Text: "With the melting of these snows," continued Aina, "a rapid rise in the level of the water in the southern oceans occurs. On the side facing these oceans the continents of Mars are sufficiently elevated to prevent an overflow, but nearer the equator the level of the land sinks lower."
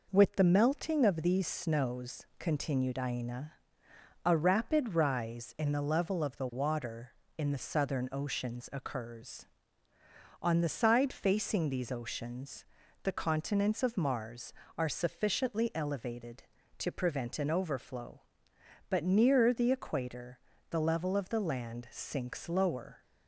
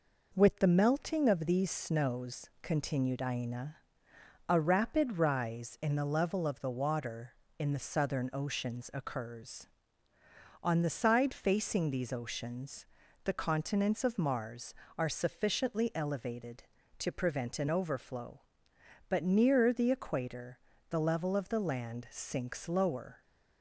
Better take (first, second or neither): neither